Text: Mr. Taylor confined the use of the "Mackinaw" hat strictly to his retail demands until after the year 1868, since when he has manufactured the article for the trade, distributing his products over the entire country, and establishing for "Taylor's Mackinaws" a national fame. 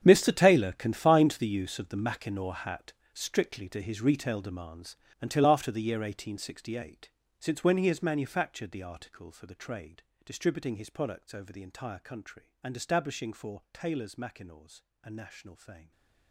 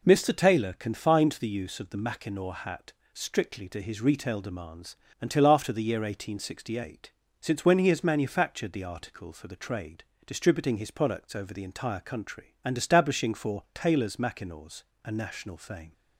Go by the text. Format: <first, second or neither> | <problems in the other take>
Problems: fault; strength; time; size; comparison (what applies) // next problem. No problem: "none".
second | gets quieter; strong; throughout; 15.5 dB // pauses between "hat" and "strictly"; slight; at 2.9 s; 0.22 s long; slight in the second // pauses between "demands" and "until"; slight; at 4.9 s; 0.24 s long; slight in the second // pauses between "Mackinaws" and "a"; slight; at 14.8 s; 0.22 s long; slight in the second // stays silent after the last word; slight; from 15.7 s on; 0.6 s long